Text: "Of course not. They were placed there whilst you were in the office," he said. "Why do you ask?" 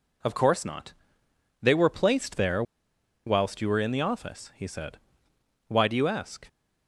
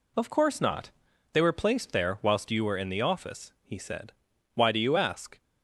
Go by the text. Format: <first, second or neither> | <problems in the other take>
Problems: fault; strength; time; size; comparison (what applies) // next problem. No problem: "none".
second | pauses between "there" and "whilst"; noticeable; at 2.6 s; 0.64 s long